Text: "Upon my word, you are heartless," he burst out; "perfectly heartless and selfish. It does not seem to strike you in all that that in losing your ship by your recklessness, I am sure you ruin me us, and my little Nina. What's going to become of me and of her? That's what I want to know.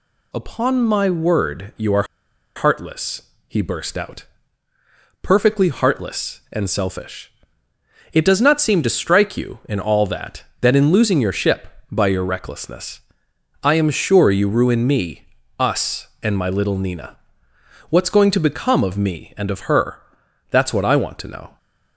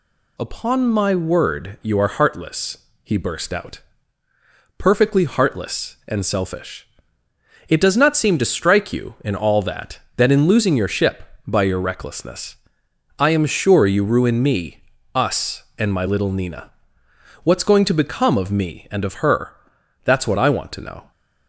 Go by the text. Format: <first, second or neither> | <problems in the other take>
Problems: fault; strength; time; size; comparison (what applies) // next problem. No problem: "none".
second | pauses between "are" and "heartless"; noticeable; at 2.0 s; 0.52 s long // pauses between "me" and "us"; slight; at 15.2 s; 0.32 s long; slight in the second